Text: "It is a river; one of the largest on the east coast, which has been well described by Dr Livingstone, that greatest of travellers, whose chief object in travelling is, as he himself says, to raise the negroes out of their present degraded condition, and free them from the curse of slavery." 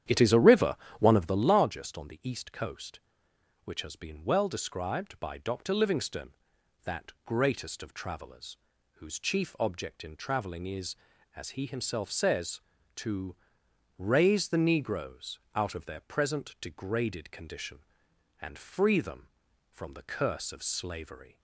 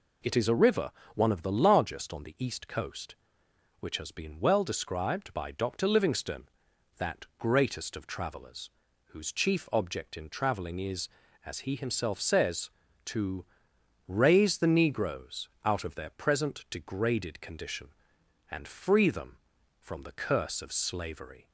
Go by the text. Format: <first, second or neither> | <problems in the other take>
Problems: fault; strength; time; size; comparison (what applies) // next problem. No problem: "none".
second | starts louder than the rest; strong; until 1.6 s; 10 dB // pauses between "to" and "raise"; noticeable; at 13.3 s; 0.60 s long; noticeable in the second // pauses between "negroes" and "out"; slight; at 15.3 s; 0.16 s long; slight in the second